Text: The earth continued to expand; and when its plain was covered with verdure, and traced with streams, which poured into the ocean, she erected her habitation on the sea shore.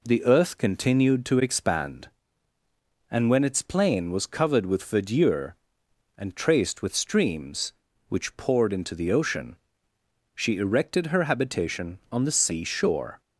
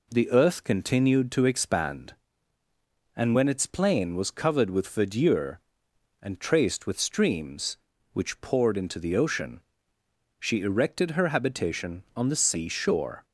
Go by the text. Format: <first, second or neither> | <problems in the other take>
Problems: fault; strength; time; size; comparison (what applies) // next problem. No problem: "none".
neither | none